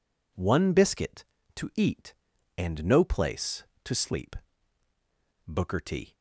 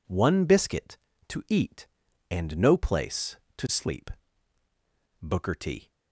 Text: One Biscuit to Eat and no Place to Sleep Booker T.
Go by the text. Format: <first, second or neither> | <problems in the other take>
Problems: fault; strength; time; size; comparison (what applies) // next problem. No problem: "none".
neither | pauses between "Sleep" and "Booker"; the same in both